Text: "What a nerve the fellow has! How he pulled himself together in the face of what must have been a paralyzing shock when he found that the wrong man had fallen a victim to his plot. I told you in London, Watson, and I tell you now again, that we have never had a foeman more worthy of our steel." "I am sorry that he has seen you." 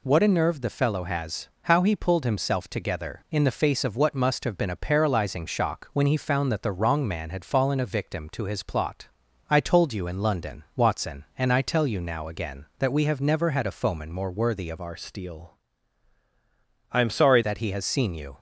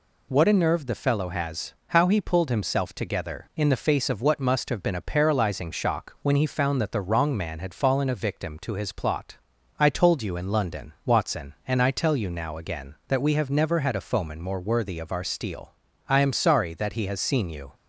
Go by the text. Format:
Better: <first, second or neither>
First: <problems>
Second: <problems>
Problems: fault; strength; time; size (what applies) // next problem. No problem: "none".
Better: second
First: changes voice from "our" to "sorry"; from 14.8 to 17.4 s; 2.6 s long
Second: none